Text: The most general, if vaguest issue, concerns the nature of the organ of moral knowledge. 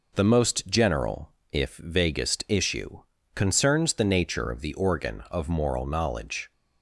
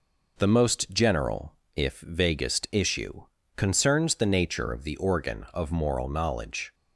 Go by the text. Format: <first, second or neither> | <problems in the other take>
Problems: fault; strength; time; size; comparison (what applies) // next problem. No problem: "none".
neither | none